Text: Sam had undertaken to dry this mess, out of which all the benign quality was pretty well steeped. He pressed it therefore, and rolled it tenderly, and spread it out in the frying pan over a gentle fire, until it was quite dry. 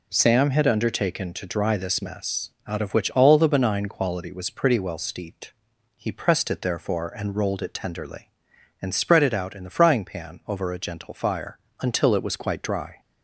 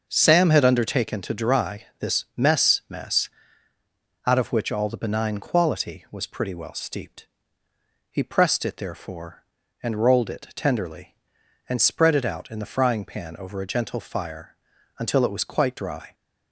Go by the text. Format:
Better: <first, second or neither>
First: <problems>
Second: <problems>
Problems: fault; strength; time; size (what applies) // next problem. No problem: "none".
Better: first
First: none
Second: starts louder than the rest; until 1.0 s; 6 dB // says "mess" twice; at 2.8 s